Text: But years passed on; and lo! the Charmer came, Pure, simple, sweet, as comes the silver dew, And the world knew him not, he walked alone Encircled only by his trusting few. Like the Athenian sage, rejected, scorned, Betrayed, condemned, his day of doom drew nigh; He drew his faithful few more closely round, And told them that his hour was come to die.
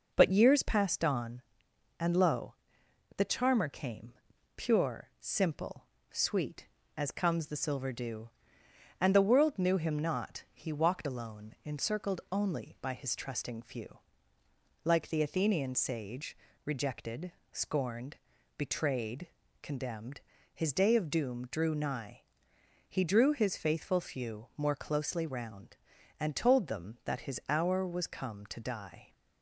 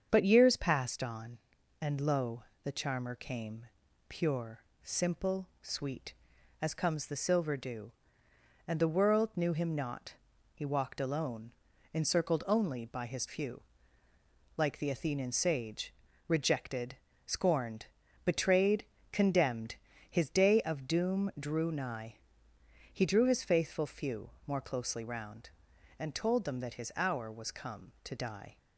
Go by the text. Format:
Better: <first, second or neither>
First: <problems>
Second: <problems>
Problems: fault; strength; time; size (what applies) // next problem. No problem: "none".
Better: first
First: none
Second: starts louder than the rest; strong; until 1.1 s; 7 dB // pauses between "alone" and "Encircled"; at 11.5 s; 0.42 s long // skips "trusting"; at 13.2 s // pauses between "few" and "more"; slight; at 24.2 s; 0.16 s long